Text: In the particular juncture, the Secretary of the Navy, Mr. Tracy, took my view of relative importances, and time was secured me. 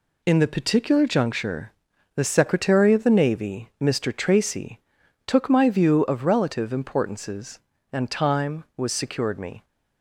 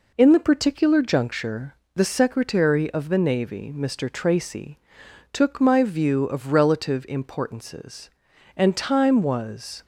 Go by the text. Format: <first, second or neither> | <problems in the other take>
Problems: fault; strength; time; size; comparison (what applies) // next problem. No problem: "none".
first | stops before "secured me"; at 9.8 s